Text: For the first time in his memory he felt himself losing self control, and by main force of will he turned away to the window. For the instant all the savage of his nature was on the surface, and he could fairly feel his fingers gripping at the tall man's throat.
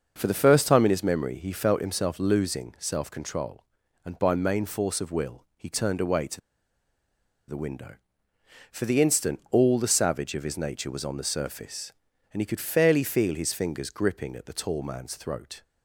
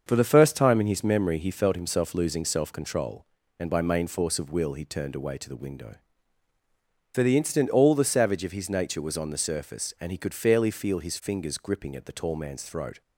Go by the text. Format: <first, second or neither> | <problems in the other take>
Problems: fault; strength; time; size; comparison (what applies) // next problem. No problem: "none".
second | starts louder than the rest; until 1.1 s; 6 dB; also in the second // pauses between "to" and "the"; at 6.4 s; 1.0 s long